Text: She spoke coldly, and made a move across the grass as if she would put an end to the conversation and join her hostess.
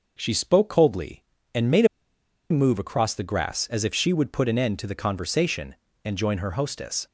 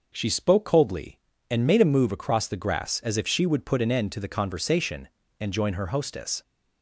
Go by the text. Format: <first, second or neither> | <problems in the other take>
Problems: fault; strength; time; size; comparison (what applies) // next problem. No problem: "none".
second | pauses between "made" and "a"; noticeable; at 1.8 s; 0.64 s long